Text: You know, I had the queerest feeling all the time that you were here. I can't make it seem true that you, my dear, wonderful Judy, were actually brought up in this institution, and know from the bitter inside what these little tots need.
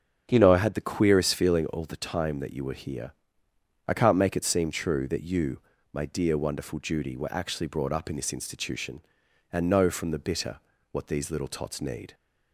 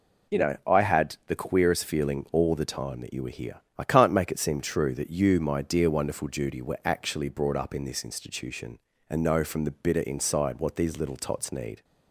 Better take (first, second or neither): second